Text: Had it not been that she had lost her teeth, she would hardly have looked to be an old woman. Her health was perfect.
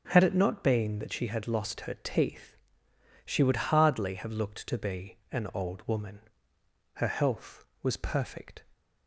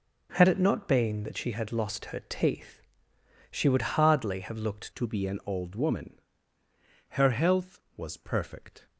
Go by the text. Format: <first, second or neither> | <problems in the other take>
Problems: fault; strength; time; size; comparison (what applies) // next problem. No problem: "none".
first | changes voice at "to"; from 4.9 s on; 3.9 s long